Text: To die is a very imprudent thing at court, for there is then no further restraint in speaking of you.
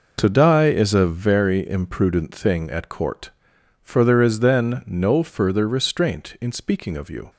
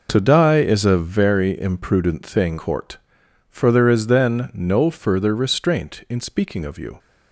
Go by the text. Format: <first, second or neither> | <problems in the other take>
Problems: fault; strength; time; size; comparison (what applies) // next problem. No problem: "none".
first | skips "at"; at 2.5 s